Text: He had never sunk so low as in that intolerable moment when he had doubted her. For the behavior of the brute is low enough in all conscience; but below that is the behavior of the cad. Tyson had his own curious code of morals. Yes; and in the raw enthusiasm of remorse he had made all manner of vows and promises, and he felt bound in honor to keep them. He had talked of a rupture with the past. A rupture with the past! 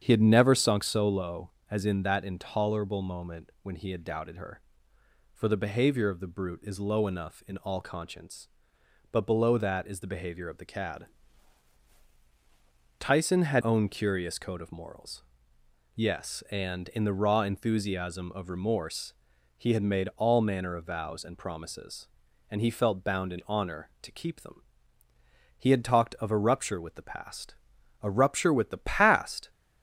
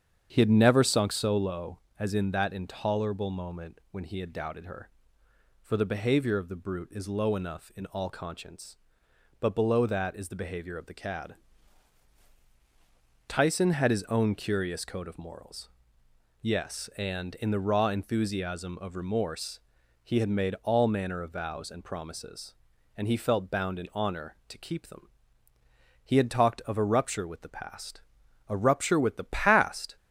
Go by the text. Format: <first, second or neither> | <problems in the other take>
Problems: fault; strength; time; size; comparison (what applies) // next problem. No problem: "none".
second | starts louder than the rest; strong; until 1.0 s; 8 dB; strong in the second // skips "his"; at 13.6 s // pauses between "remorse" and "he"; noticeable; at 19.1 s; 0.46 s long; noticeable in the second